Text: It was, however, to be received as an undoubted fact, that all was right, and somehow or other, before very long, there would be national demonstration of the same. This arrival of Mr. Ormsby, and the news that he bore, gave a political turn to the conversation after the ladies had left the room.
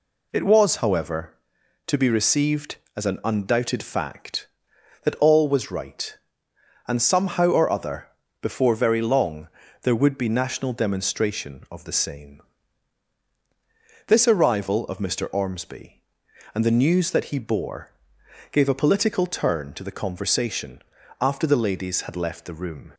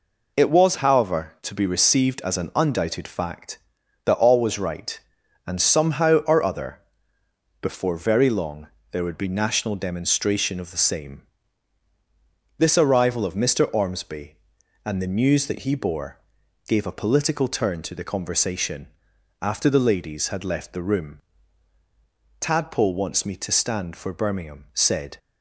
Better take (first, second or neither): first